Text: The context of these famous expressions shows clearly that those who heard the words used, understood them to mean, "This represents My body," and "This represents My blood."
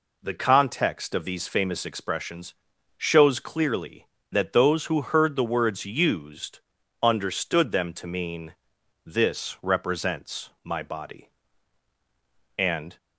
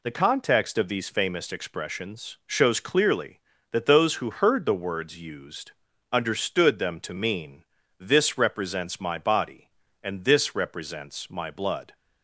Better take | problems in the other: second | pauses between "expressions" and "shows"; at 2.5 s; 0.44 s long // pauses between "represents" and "My"; slight; at 10.4 s; 0.16 s long // stops before "This represents My blood"; at 12.9 s

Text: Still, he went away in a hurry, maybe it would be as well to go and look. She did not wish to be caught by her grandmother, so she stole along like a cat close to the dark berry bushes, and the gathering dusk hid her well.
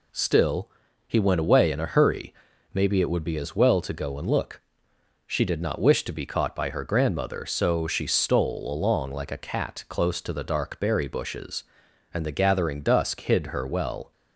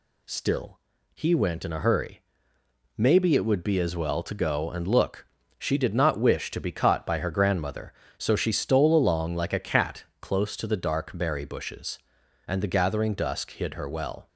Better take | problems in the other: first | skips "away"; at 1.6 s // pauses between "cat" and "close"; slight; at 10.0 s; 0.16 s long

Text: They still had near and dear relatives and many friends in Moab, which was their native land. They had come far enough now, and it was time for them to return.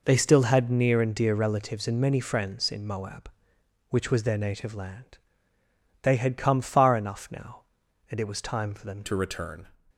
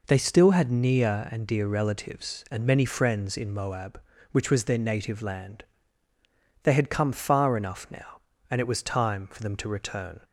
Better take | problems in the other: second | changes voice at "to"; from 9.0 s on; 0.6 s long

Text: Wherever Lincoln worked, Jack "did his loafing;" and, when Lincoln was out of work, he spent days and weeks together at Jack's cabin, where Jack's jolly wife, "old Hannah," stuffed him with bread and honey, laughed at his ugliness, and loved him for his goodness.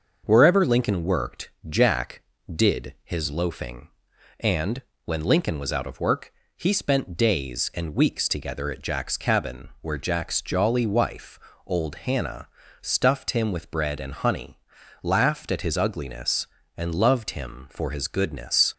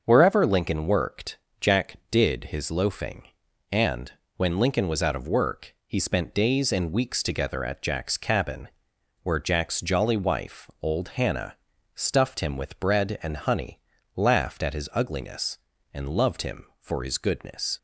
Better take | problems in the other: neither | starts louder than the rest; the same in both

